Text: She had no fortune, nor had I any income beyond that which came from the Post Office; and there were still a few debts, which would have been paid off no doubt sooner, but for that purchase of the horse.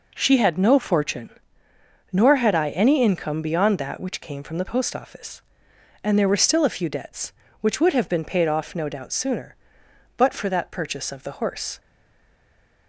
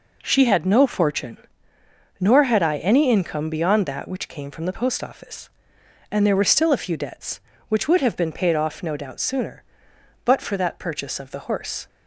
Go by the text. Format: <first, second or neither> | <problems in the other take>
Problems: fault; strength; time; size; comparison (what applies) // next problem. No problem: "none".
second | stays silent after the last word; from 11.7 s on; 1.1 s long